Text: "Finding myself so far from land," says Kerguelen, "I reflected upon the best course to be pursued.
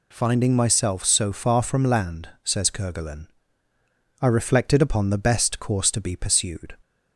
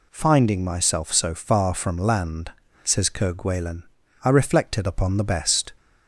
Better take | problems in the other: first | stops before "course to be pursued"; at 5.7 s

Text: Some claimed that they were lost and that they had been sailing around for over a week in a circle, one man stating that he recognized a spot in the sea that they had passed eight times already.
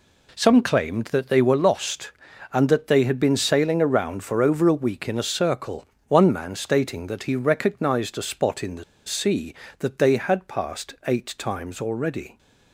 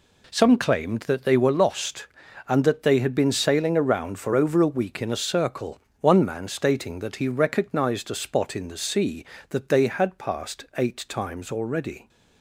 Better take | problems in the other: second | pauses between "the" and "sea"; slight; at 8.8 s; 0.23 s long

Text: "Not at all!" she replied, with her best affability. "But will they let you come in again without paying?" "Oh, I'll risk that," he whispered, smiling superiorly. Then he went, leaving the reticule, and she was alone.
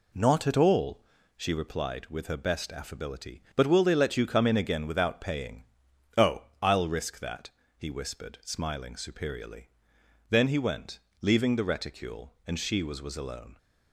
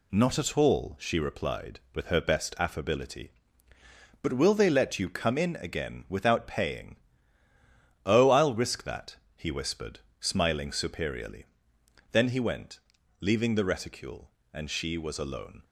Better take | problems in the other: second | says "was" twice; at 13.0 s

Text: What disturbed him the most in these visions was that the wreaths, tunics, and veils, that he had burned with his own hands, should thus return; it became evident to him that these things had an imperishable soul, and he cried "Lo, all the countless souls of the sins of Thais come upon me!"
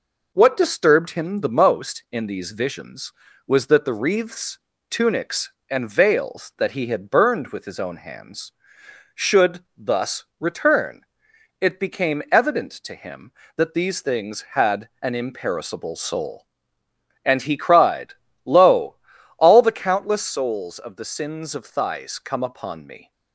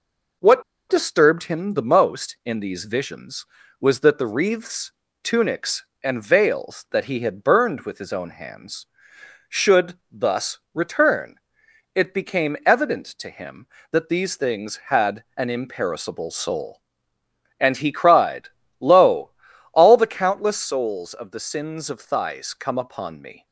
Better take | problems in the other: first | pauses between "What" and "disturbed"; slight; at 0.6 s; 0.27 s long // pauses between "thus" and "return"; slight; at 10.5 s; 0.16 s long; slight in the first // pauses between "had" and "an"; slight; at 15.2 s; 0.16 s long; slight in the first // pauses between "cried" and "Lo"; slight; at 18.4 s; 0.32 s long; slight in the first

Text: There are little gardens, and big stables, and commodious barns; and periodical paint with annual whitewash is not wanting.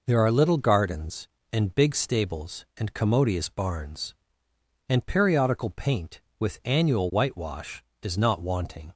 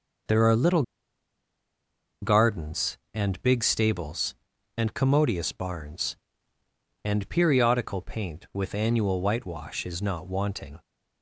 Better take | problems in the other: first | starts louder than the rest; noticeable; until 2.6 s; 6 dB // pauses between "little" and "gardens"; strong; at 0.8 s; 1.3 s long

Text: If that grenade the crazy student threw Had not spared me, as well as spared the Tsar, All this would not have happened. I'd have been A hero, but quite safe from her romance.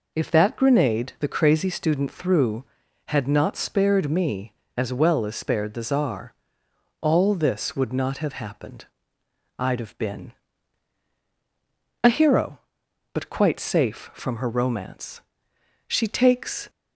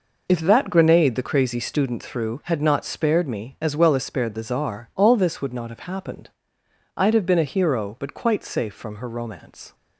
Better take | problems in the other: second | pauses between "been" and "A"; strong; at 10.3 s; 1.7 s long // goes on to say "She takes"; noticeable; from 15.8 s on; 0.82 s long

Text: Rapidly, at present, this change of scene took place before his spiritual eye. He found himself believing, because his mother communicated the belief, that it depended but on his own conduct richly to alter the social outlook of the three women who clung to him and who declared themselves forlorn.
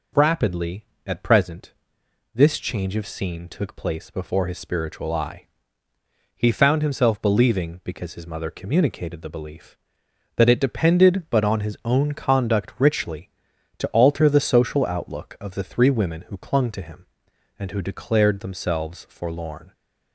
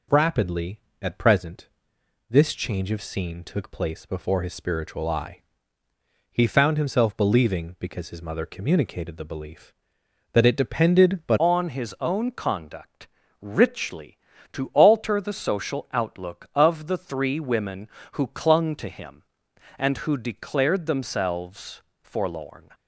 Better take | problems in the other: first | changes voice at "on"; from 11.3 s on; 11.4 s long // pauses between "conduct" and "richly"; slight; at 13.0 s; 0.34 s long // pauses between "themselves" and "forlorn"; slight; at 21.8 s; 0.20 s long

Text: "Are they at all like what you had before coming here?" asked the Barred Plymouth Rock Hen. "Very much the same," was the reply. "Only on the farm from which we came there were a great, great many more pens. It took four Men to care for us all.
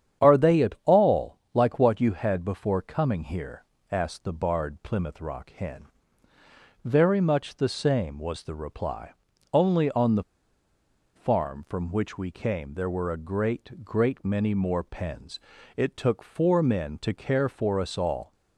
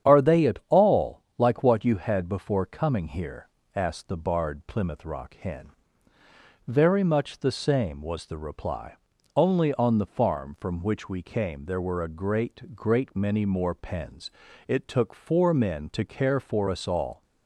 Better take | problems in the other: second | starts louder than the rest; strong; until 1.3 s; 9 dB; strong in the second // pauses between "the" and "farm"; noticeable; at 10.2 s; 0.92 s long

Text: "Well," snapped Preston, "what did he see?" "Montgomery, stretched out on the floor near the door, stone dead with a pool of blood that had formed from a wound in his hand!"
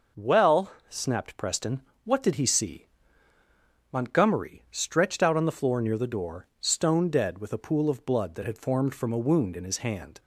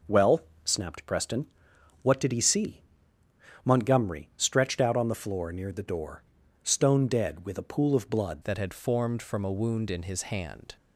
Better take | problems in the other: first | changes voice at "that"; from 8.4 s on; 2.3 s long

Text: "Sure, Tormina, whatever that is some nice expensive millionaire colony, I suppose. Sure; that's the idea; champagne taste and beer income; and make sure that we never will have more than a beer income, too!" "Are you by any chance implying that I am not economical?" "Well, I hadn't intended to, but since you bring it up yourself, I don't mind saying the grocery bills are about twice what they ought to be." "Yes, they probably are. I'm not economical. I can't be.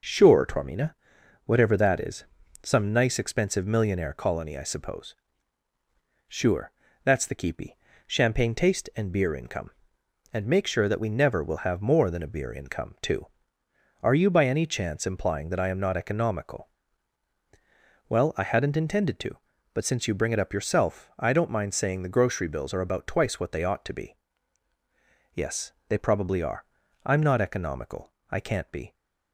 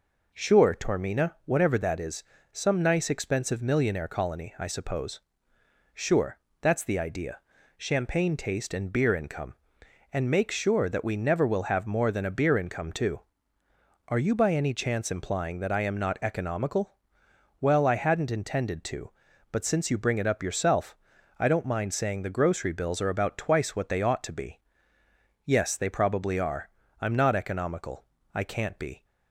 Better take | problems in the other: second | pauses between "is" and "some"; at 2.2 s; 0.38 s long; slight in the second // says "keepy" for "idea"; at 7.3 s

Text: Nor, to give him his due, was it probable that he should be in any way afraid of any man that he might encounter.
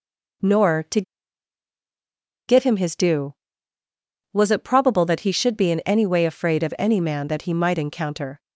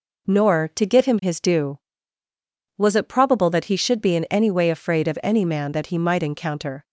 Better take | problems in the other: second | pauses between "to" and "give"; strong; at 1.0 s; 1.4 s long

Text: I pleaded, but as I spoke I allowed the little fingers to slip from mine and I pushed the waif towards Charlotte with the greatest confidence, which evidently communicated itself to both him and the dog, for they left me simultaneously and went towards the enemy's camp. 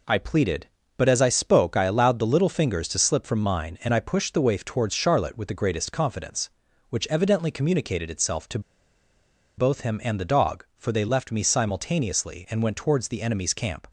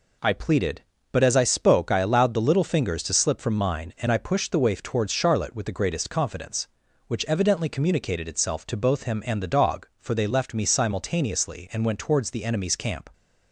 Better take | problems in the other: second | pauses between "to" and "both"; at 8.5 s; 0.98 s long

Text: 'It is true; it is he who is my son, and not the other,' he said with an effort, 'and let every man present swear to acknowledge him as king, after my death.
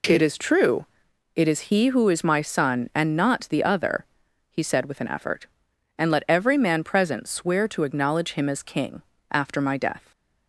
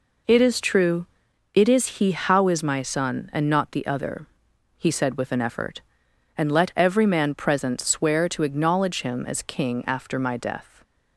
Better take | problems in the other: first | says "how" for "who"; at 2.1 s

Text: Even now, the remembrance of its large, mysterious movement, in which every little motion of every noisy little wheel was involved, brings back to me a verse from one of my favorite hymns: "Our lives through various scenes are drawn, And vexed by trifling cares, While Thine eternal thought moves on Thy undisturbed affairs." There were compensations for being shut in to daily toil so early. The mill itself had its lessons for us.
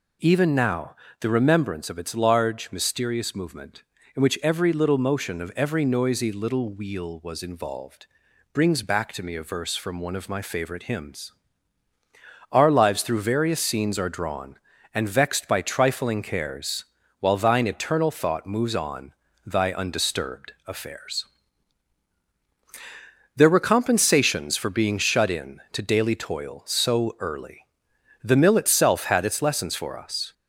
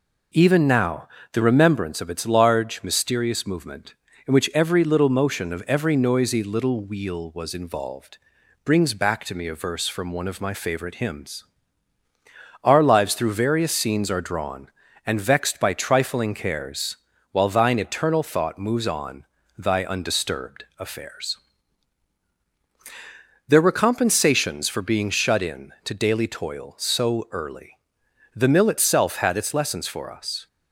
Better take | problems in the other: second | gets louder; slight; throughout; 2.5 dB // pauses between "on" and "Thy"; slight; at 19.1 s; 0.34 s long; slight in the second // pauses between "undisturbed" and "affairs"; slight; at 20.5 s; 0.16 s long; slight in the second

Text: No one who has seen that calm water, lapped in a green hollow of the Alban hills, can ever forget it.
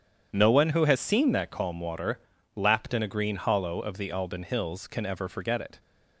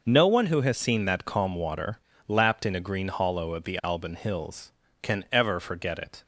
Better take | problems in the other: second | starts louder than the rest; strong; until 1.6 s; 8.5 dB

